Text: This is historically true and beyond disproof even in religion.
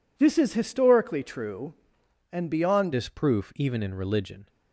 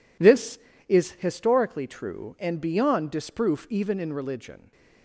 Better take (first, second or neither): second